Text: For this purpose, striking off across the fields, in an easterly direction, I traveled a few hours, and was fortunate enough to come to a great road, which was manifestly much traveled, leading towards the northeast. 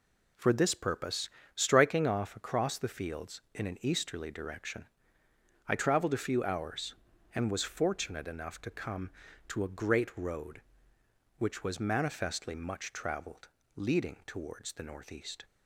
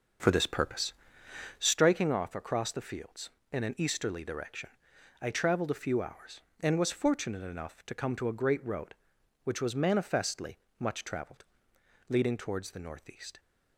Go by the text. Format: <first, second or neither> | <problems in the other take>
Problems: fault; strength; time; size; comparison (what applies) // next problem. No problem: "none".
first | starts louder than the rest; noticeable; until 1.8 s; 6 dB // pauses between "manifestly" and "much"; slight; at 10.5 s; 0.20 s long